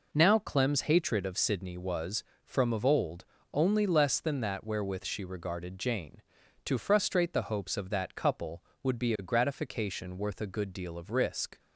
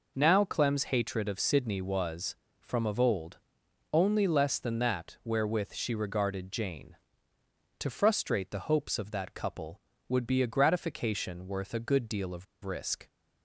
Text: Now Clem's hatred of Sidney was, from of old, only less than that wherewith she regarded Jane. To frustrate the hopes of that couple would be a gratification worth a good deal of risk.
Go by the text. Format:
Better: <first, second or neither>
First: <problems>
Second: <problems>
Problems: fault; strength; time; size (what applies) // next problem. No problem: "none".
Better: first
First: none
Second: pauses between "of" and "risk"; slight; at 12.4 s; 0.19 s long